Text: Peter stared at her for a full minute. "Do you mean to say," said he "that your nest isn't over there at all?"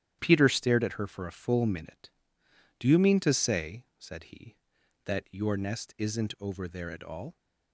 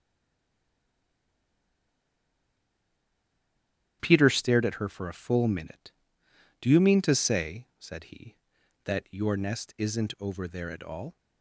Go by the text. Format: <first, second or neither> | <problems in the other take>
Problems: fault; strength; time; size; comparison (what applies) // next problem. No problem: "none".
first | stays silent before the first word; strong; until 4.0 s; 4.0 s long // starts louder than the rest; strong; until 5.0 s; 11 dB; strong in the first